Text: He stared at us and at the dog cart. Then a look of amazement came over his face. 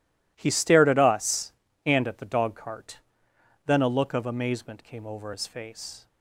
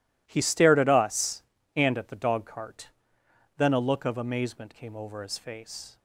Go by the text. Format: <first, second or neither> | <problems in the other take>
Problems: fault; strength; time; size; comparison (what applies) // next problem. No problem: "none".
neither | none